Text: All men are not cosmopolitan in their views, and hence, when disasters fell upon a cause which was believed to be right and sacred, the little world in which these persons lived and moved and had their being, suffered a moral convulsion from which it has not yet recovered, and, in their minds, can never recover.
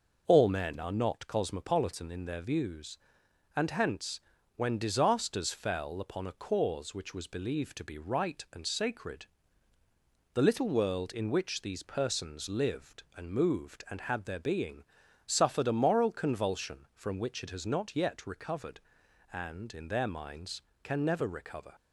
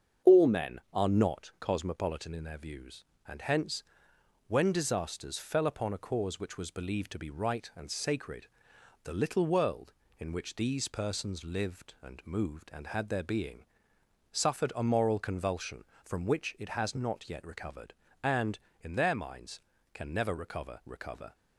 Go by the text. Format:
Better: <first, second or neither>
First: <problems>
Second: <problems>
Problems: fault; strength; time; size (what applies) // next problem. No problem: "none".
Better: first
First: none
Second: starts louder than the rest; strong; until 1.4 s; 7.5 dB // says "recover" twice; at 20.8 s